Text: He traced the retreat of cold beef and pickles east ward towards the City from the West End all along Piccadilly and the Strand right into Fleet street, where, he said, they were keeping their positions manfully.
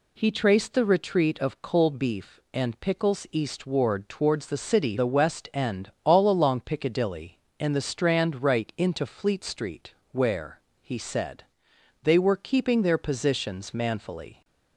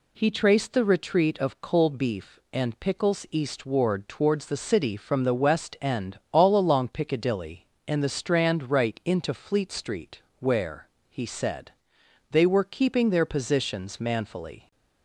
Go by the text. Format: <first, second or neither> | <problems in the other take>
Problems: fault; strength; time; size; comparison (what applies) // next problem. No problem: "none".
second | skips "from"; at 4.9 s